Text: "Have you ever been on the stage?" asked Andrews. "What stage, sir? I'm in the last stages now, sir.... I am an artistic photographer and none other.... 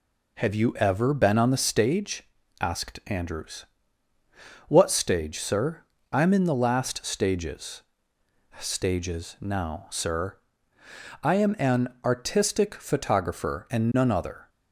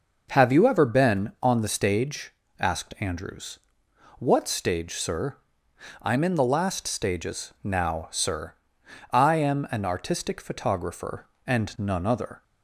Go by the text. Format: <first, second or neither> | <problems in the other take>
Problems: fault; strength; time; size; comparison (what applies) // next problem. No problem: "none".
second | says "stages" twice; at 8.5 s // pauses between "an" and "artistic"; slight; at 11.8 s; 0.18 s long